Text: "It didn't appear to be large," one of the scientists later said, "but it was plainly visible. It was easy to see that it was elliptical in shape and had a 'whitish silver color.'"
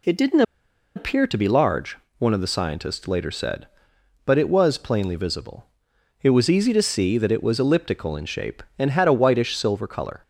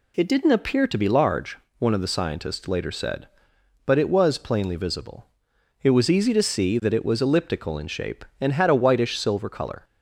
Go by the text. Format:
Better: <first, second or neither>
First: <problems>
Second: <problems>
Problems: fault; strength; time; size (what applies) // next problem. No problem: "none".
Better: second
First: pauses between "didn't" and "appear"; noticeable; at 0.4 s; 0.53 s long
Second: none